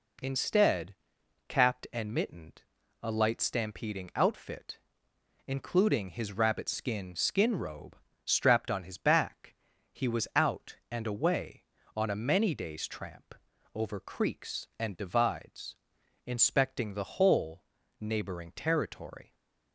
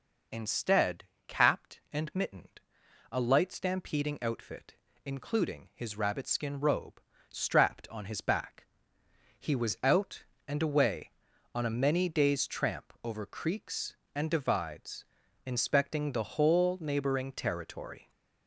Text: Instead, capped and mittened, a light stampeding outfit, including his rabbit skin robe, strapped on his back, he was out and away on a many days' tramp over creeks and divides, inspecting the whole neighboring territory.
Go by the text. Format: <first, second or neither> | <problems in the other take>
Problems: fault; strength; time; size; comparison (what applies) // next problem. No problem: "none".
second | says "skin" twice; at 7.1 s // pauses between "tramp" and "over"; at 13.3 s; 0.40 s long // pauses between "whole" and "neighboring"; slight; at 17.6 s; 0.36 s long